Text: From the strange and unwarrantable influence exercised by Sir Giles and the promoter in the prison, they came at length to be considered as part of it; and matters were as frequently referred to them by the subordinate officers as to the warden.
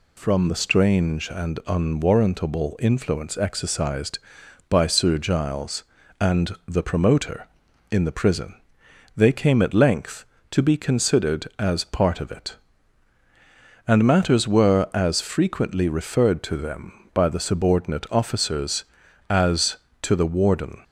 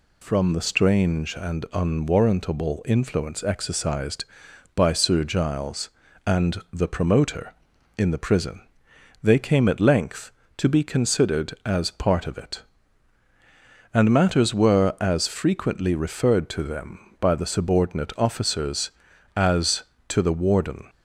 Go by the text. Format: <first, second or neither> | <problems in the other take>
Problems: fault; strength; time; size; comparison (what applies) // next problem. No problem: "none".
neither | none